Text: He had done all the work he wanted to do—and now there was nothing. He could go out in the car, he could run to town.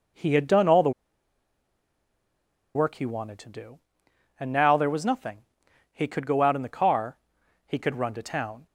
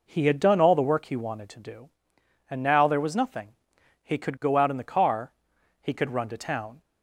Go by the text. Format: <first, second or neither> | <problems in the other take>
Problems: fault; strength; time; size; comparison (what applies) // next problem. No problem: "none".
second | pauses between "the" and "work"; strong; at 0.9 s; 1.8 s long